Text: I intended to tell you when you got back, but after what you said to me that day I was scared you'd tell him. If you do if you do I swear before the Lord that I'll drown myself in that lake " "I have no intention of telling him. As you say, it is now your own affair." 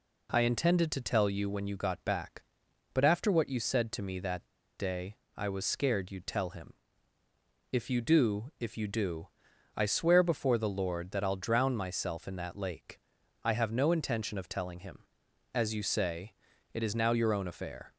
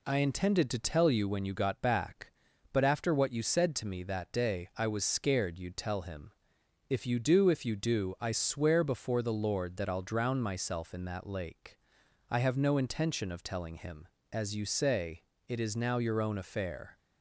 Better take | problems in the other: second | pauses between "that" and "day"; slight; at 4.4 s; 0.30 s long // pauses between "day" and "I"; slight; at 5.1 s; 0.20 s long // pauses between "do" and "I"; noticeable; at 9.2 s; 0.46 s long

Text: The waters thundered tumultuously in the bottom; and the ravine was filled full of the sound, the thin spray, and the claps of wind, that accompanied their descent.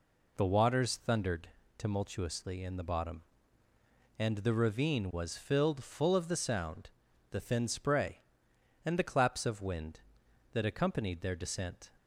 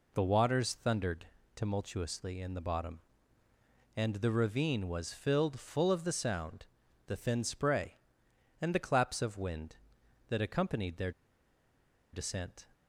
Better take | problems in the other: first | pauses between "thundered" and "tumultuously"; slight; at 1.2 s; 0.28 s long; slight in the first // pauses between "their" and "descent"; at 11.1 s; 1.0 s long

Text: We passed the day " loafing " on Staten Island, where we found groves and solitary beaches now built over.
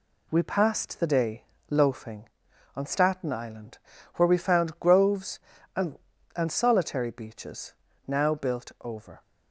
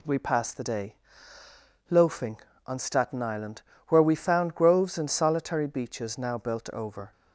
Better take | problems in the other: second | says "and" twice; at 6.3 s // pauses between "beaches" and "now"; slight; at 7.7 s; 0.34 s long

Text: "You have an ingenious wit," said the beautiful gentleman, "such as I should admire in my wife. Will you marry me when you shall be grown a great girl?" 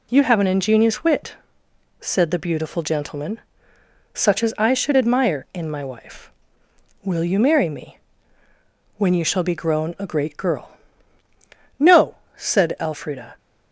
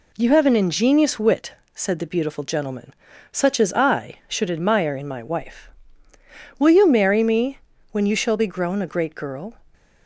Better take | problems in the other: second | pauses between "me" and "when"; noticeable; at 7.9 s; 0.98 s long; slight in the second // goes on to say "No said Elfrida"; from 11.7 s on; 1.5 s long

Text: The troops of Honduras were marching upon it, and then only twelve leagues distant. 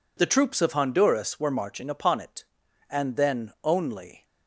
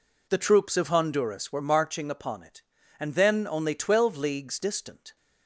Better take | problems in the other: second | stops before "twelve leagues distant"; at 4.2 s

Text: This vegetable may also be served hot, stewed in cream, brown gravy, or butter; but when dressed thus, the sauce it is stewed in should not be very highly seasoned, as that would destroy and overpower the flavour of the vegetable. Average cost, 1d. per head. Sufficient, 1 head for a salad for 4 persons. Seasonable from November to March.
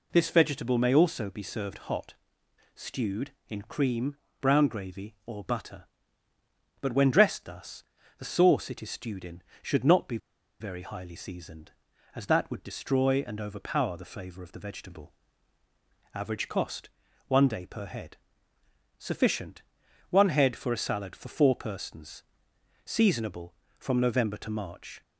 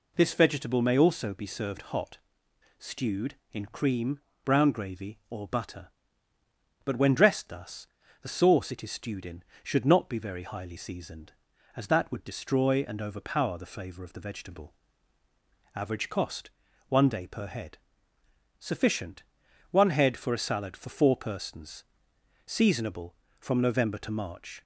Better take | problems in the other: second | pauses between "be" and "very"; at 10.1 s; 0.43 s long

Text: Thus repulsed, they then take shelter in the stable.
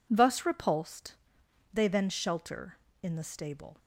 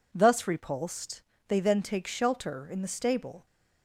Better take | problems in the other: second | skips "take"; at 2.0 s

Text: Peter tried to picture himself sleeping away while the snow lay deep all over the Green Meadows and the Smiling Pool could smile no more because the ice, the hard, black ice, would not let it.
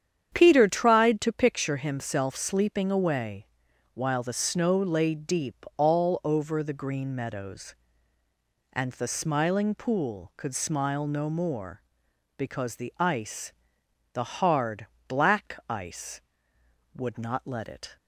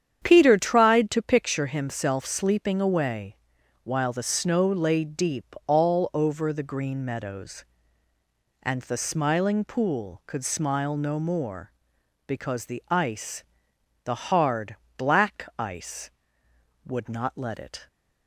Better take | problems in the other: neither | starts louder than the rest; strong; the same in both // pauses between "away" and "while"; noticeable; the same in both

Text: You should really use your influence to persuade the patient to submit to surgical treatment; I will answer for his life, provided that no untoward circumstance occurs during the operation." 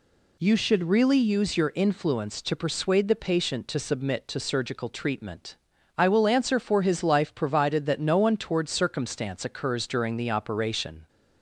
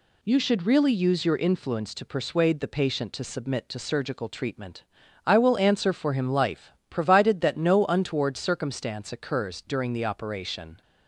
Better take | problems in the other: first | says "him" for "his"; at 6.1 s

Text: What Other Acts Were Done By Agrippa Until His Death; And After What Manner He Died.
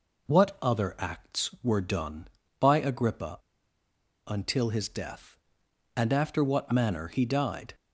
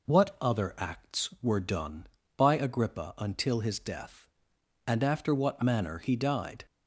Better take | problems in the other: second | pauses between "Agrippa" and "Until"; noticeable; at 3.3 s; 0.89 s long

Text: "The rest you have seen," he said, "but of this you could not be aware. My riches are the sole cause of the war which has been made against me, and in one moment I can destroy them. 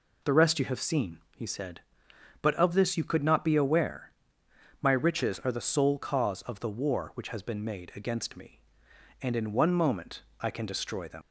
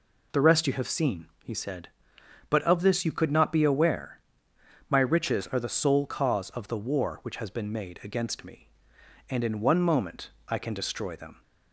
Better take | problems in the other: second | pauses between "moment" and "I"; slight; at 10.2 s; 0.16 s long; slight in the second // leaves "them" unfinished; at 11.2 s; 120 ms

